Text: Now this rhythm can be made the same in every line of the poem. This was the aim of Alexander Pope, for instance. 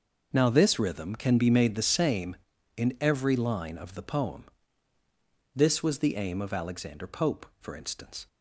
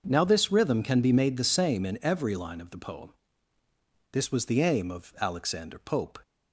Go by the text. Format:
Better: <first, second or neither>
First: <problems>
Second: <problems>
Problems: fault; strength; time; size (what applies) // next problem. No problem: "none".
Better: first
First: none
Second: starts louder than the rest; noticeable; until 1.0 s; 6 dB // stops before "for instance"; at 6.2 s